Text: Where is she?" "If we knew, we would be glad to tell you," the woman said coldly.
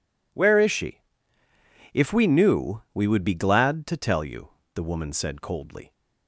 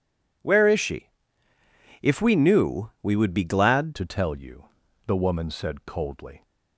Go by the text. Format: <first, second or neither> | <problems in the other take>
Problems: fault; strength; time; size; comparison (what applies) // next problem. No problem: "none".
first | changes voice at "to"; from 3.9 s on; 2.5 s long